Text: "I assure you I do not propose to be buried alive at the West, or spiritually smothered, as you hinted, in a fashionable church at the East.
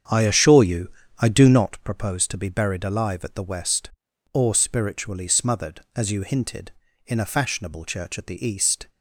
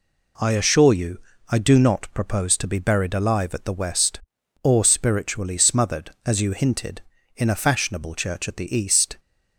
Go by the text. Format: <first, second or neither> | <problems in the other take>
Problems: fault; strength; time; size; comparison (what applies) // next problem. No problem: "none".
second | starts louder than the rest; strong; until 1.7 s; 7.5 dB // pauses between "you" and "I"; slight; at 0.8 s; 0.30 s long; slight in the second